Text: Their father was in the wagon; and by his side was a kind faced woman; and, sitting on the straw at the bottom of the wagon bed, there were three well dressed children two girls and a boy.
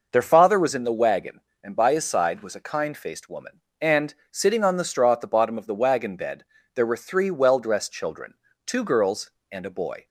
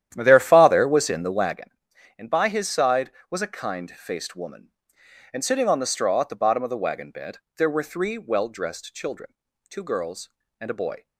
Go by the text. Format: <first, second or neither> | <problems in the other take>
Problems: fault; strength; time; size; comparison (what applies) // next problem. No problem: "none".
first | starts louder than the rest; strong; until 1.6 s; 11 dB // pauses between "children" and "two"; slight; at 9.3 s; 0.36 s long; slight in the first